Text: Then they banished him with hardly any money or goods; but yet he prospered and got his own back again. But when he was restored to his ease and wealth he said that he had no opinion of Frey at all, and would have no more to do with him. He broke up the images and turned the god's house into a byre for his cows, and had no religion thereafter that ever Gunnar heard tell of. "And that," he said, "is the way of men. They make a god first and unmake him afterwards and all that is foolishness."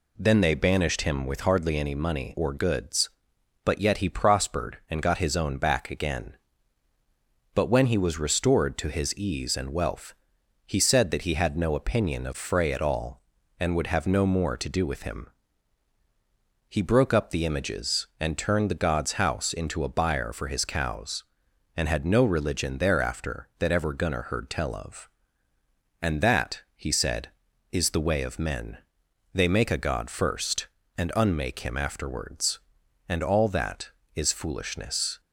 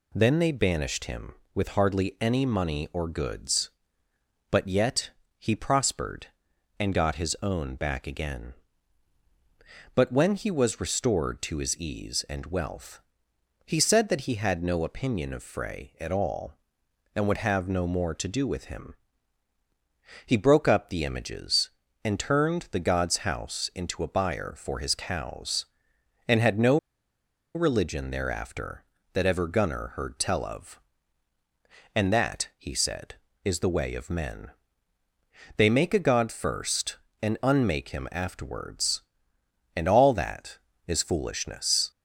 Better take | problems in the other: first | pauses between "yet" and "he"; slight; at 5.1 s; 0.28 s long // pauses between "wealth" and "he"; noticeable; at 13.0 s; 0.64 s long; noticeable in the first // pauses between "no" and "religion"; noticeable; at 26.7 s; 0.78 s long

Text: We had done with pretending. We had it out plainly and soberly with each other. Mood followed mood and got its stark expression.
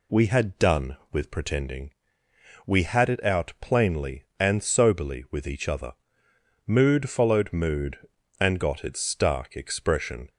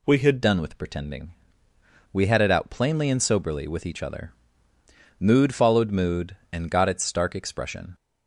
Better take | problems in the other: first | changes voice at "done"; from 0.4 s on; 7.5 s long

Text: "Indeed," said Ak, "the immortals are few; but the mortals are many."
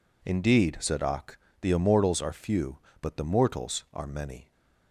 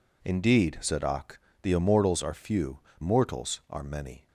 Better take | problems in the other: first | skips "but the"; at 2.8 s

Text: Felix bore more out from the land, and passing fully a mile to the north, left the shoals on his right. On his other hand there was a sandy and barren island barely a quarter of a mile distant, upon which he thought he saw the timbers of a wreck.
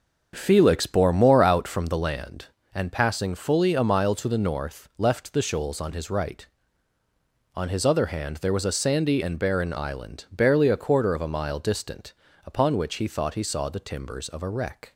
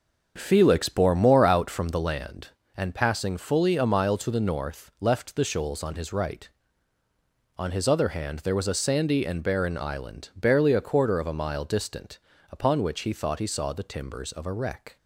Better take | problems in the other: neither | starts louder than the rest; the same in both

